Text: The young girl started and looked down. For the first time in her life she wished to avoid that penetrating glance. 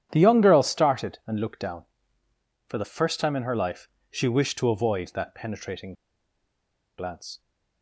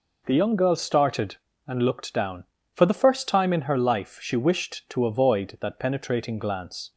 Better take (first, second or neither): second